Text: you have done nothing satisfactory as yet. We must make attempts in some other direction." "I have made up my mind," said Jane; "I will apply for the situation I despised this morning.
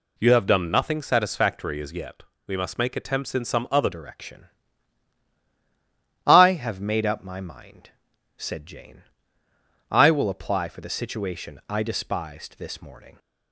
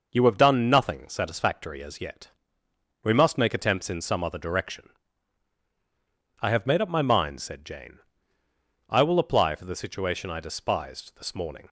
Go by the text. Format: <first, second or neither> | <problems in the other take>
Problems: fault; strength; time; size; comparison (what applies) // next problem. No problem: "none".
second | changes voice at "direction"; from 3.9 s on; 9.2 s long